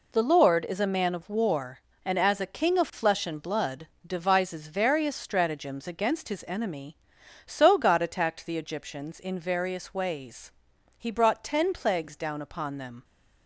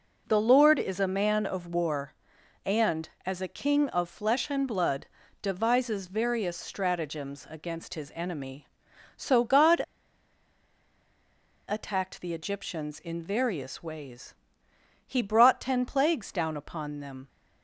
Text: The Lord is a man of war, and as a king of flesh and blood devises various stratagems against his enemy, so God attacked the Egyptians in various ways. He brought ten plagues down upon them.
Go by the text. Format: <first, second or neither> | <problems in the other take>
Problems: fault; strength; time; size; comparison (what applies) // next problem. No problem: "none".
first | pauses between "blood" and "devises"; at 5.0 s; 0.38 s long; slight in the first // pauses between "God" and "attacked"; strong; at 9.8 s; 1.8 s long